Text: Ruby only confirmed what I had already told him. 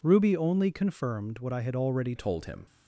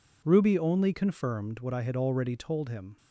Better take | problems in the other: second | changes voice at "told"; from 2.1 s on; 0.5 s long

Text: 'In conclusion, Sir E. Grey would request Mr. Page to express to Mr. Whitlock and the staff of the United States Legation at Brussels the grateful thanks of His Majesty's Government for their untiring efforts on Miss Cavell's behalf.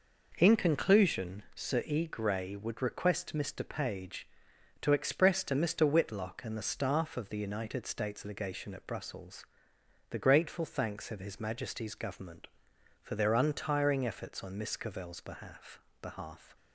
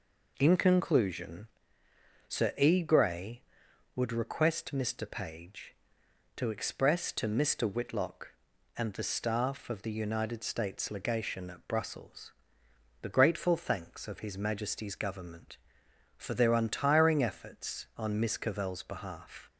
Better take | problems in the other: second | pauses between "Brussels" and "the"; noticeable; at 9.4 s; 0.64 s long; noticeable in the second // says "behalf" twice; at 16.0 s

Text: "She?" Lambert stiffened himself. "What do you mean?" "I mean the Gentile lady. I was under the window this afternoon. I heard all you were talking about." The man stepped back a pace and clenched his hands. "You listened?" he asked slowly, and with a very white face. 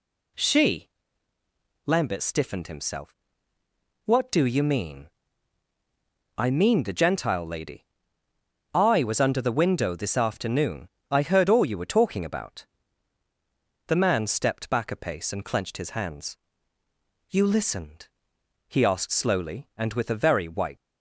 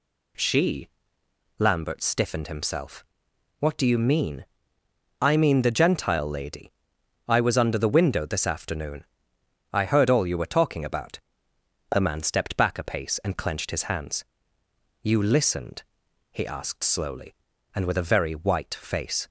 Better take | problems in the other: second | stops before "face"; at 20.7 s

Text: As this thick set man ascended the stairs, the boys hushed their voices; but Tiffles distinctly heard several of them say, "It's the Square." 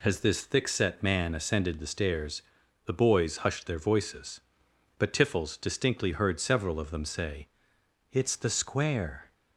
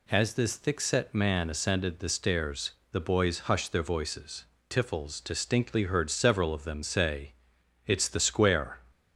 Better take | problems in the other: first | skips "but"; at 4.5 s

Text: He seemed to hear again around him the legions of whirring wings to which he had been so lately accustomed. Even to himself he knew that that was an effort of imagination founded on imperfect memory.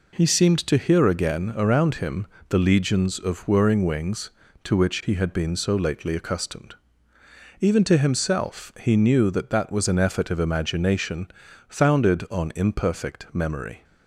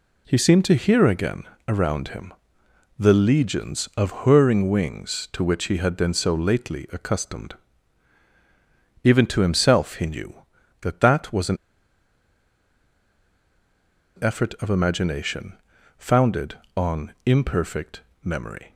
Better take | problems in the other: first | pauses between "again" and "around"; slight; at 1.4 s; 0.26 s long // pauses between "him" and "the"; noticeable; at 2.3 s; 0.66 s long; slight in the first // pauses between "an" and "effort"; strong; at 11.5 s; 2.6 s long // pauses between "imagination" and "founded"; at 15.5 s; 0.44 s long; also in the first // pauses between "imperfect" and "memory"; slight; at 18.0 s; 0.20 s long

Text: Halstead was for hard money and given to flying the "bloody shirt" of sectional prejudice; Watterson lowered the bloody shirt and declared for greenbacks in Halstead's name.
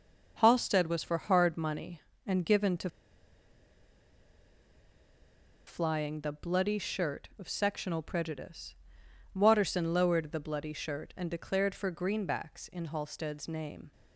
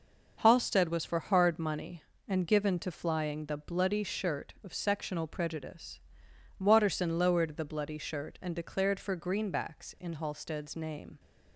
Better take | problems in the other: second | pauses between "to" and "flying"; strong; at 2.8 s; 2.7 s long

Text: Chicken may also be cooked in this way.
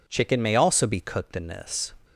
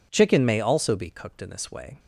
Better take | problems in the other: second | stops before "way"; at 2.0 s

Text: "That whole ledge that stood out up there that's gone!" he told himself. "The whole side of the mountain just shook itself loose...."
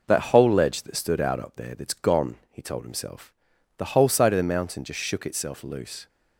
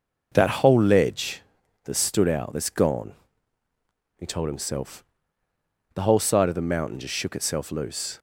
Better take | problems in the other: first | skips "up there"; at 2.5 s

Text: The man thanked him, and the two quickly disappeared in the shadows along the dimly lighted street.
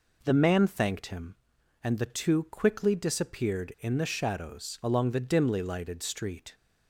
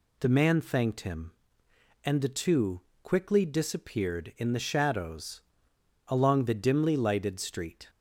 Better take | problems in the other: first | pauses between "two" and "quickly"; slight; at 2.7 s; 0.22 s long // pauses between "shadows" and "along"; noticeable; at 5.4 s; 0.64 s long

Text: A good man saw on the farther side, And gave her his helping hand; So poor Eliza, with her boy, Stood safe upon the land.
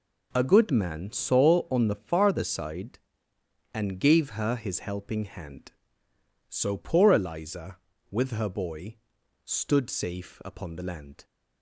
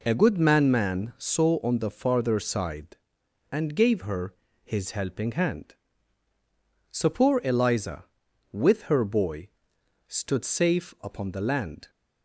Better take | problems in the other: first | says "man" twice; at 0.7 s // pauses between "her" and "his"; slight; at 4.3 s; 0.30 s long

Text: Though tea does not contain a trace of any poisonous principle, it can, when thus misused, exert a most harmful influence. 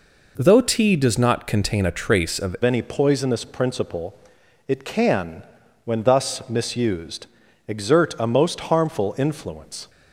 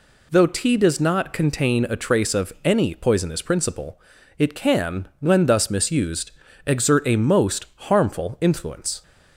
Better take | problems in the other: second | changes voice at "any"; from 2.6 s on; 7.2 s long

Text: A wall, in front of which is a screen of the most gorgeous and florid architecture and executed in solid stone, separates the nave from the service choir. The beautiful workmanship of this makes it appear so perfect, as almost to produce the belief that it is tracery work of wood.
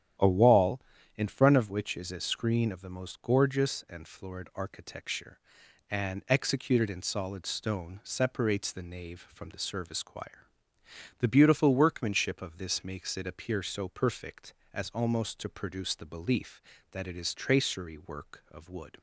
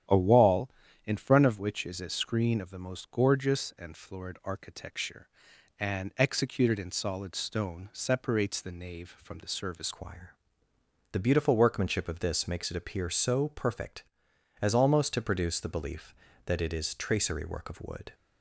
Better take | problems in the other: first | starts louder than the rest; strong; until 1.4 s; 10 dB; strong in the first // changes voice at "choir"; from 9.9 s on; 8.2 s long

